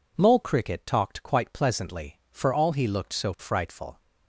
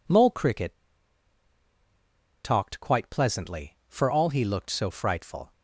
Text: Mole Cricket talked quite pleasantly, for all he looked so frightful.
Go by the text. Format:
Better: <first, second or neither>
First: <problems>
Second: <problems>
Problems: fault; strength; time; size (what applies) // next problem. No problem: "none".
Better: first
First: none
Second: pauses between "Cricket" and "talked"; strong; at 0.7 s; 1.6 s long